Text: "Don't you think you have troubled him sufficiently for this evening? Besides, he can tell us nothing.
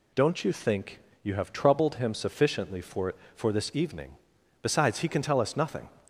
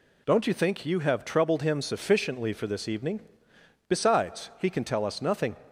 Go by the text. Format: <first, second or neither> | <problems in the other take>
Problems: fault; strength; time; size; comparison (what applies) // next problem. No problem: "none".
second | pauses between "think" and "you"; slight; at 0.9 s; 0.24 s long // says "for" twice; at 3.3 s